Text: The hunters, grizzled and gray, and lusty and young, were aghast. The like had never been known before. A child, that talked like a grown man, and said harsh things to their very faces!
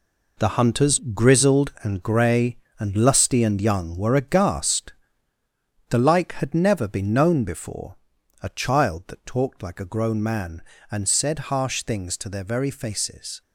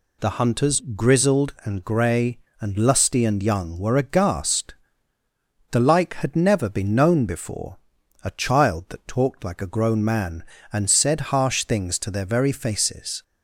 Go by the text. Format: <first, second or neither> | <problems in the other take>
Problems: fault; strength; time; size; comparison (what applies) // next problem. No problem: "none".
second | gets quieter; strong; throughout; 9.5 dB